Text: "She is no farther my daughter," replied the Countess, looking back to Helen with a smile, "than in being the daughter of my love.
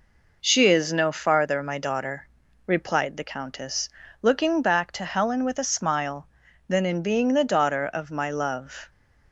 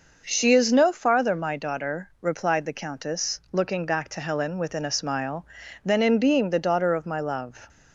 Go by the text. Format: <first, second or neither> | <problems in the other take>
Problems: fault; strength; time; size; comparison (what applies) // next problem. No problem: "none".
first | says "within" for "with"; at 4.5 s